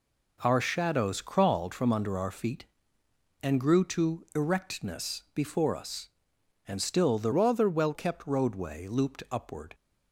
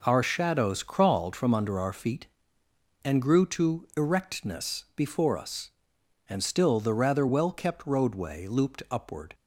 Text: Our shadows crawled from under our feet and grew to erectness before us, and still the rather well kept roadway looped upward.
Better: second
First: changes voice from "rather" to "well"; from 7.3 to 7.9 s; 0.6 s long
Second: none

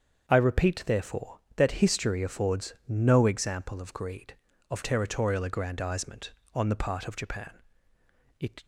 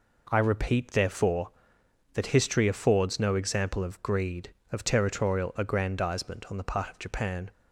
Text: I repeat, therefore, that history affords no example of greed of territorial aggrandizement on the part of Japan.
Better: second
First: starts louder than the rest; until 1.3 s; 7 dB // pauses between "affords" and "no"; slight; at 2.7 s; 0.16 s long // goes on to say "It"; slight; from 8.3 s on; 0.26 s long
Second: none

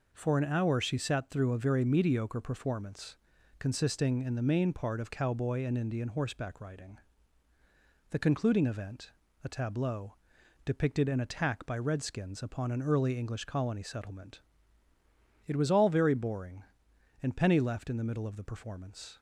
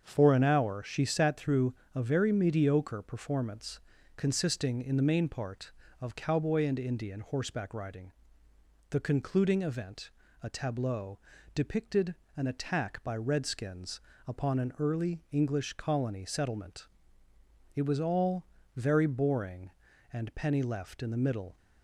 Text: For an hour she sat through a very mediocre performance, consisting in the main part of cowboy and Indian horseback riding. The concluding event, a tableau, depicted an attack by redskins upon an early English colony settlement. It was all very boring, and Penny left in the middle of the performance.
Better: first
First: none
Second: starts louder than the rest; until 1.0 s; 7 dB // pauses between "through" and "a"; slight; at 1.7 s; 0.20 s long // pauses between "depicted" and "an"; slight; at 12.1 s; 0.22 s long // pauses between "redskins" and "upon"; slight; at 13.9 s; 0.28 s long // pauses between "all" and "very"; slight; at 18.4 s; 0.30 s long // stops before "of the performance"; at 21.5 s

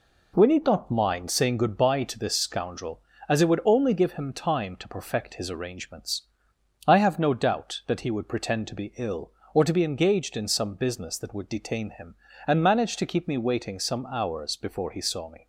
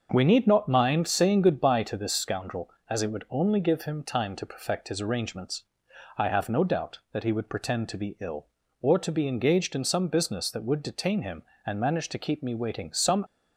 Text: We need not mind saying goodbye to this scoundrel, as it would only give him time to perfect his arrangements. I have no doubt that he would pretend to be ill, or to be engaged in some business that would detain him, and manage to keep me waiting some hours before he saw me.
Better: first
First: none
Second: starts louder than the rest; until 1.1 s; 6.5 dB // stops before "hours before he saw me"; at 13.2 s

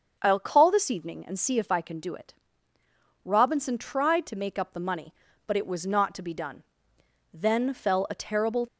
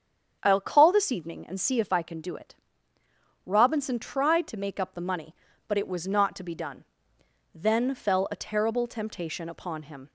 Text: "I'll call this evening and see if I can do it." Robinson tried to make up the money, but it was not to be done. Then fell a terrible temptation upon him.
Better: second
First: starts louder than the rest; until 1.2 s; 6.5 dB // stops before "temptation upon him"; at 8.6 s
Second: starts louder than the rest; strong; until 1.4 s; 7.5 dB

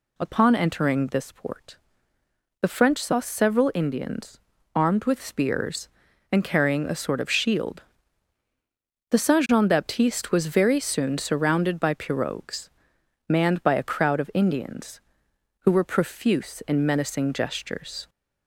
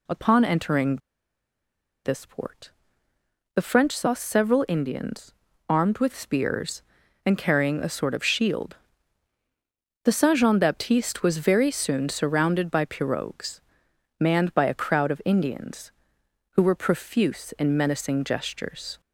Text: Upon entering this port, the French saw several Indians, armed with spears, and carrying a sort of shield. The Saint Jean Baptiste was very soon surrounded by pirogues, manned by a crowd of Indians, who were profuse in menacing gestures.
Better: first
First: none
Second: pauses between "entering" and "this"; at 0.9 s; 1.0 s long

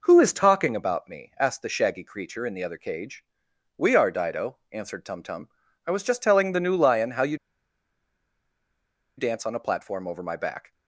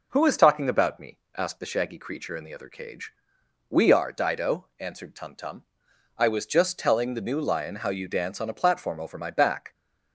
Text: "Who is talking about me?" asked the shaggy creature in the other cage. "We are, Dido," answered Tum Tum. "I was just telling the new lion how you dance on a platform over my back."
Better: second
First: pauses between "you" and "dance"; strong; at 7.3 s; 1.8 s long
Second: none

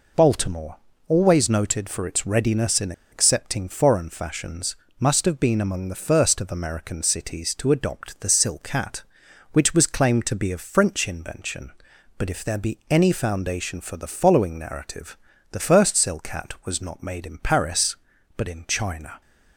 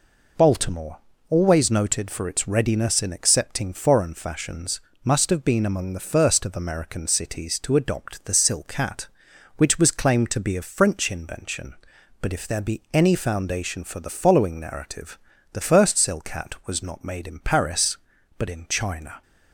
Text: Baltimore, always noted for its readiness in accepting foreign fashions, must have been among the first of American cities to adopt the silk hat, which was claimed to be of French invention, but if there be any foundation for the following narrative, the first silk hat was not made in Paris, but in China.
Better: second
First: pauses between "in" and "accepting"; slight; at 2.9 s; 0.19 s long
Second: none

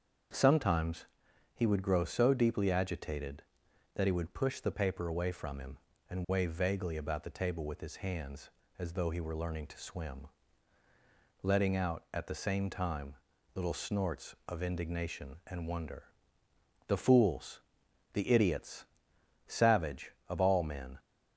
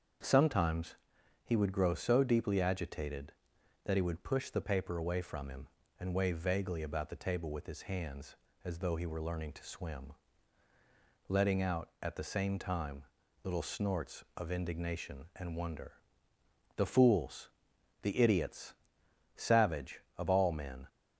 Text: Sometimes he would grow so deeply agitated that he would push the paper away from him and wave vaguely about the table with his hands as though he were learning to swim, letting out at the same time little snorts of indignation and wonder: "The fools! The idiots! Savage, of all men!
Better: neither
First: starts louder than the rest; until 1.8 s; 7 dB // pauses between "Sometimes" and "he"; noticeable; at 1.0 s; 0.50 s long // pauses between "time" and "little"; at 13.1 s; 0.40 s long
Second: starts louder than the rest; until 1.7 s; 7 dB // pauses between "Sometimes" and "he"; noticeable; at 0.9 s; 0.50 s long // pauses between "time" and "little"; at 13.0 s; 0.40 s long

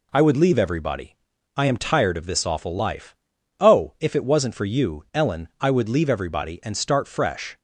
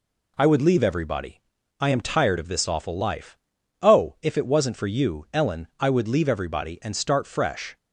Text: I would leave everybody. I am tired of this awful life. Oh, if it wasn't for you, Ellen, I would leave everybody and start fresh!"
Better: neither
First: none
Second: none

